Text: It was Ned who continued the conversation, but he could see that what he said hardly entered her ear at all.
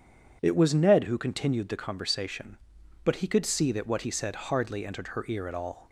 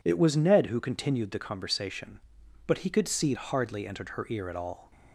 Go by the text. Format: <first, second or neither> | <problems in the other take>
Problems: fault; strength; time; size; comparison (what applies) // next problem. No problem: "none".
first | skips "that what he said"; at 3.3 s